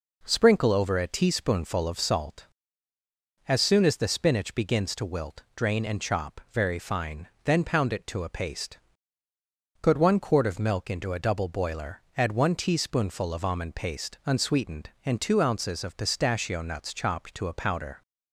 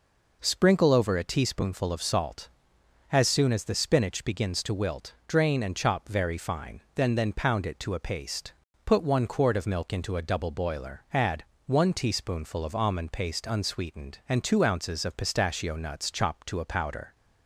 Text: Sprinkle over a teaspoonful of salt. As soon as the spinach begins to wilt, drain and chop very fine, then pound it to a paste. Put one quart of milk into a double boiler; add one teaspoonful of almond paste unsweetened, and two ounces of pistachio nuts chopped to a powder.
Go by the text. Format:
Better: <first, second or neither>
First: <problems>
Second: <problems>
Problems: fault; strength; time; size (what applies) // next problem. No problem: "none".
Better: first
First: none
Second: says "then" twice; at 7.1 s // pauses between "add" and "one"; slight; at 11.4 s; 0.22 s long